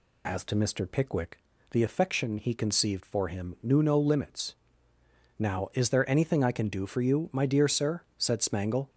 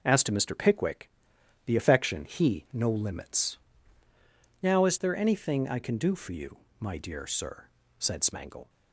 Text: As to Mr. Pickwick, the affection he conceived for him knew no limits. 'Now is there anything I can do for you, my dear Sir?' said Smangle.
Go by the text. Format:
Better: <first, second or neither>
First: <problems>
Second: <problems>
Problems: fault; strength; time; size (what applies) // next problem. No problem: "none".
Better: first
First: none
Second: skips "conceived for him knew"; at 2.6 s